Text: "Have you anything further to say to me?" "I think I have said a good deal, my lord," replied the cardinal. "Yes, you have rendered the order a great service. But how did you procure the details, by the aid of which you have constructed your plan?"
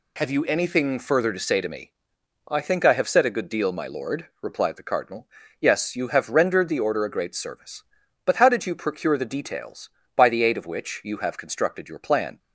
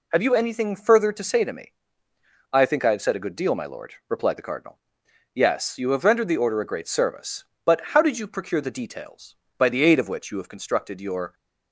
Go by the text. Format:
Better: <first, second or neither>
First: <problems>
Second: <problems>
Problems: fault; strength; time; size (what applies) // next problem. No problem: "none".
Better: first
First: none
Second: stops before "plan"; at 11.3 s